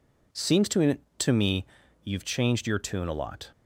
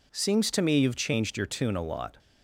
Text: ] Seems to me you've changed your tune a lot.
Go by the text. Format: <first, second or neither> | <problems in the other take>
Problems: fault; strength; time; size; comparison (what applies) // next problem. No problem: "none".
second | says "to" twice; at 1.1 s // pauses between "me" and "you've"; at 1.6 s; 0.40 s long